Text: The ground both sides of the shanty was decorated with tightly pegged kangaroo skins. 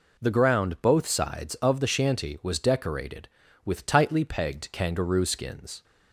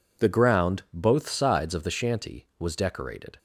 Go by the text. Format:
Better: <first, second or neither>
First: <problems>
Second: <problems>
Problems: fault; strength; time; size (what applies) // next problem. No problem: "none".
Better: first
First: none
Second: stops before "with tightly pegged kangaroo skins"; at 3.3 s